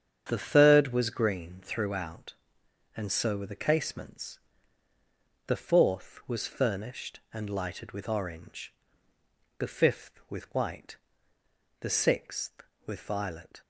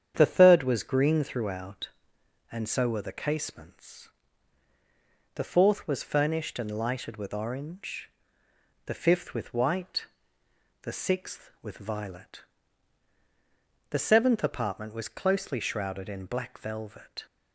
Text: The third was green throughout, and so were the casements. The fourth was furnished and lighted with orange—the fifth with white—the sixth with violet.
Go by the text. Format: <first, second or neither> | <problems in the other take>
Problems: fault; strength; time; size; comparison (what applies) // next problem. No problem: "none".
first | starts louder than the rest; strong; until 1.1 s; 8.5 dB; strong in the first // goes on to say "The seventh apartment was closely shrouded in black velvet"; strong; from 13.8 s on; 3.3 s long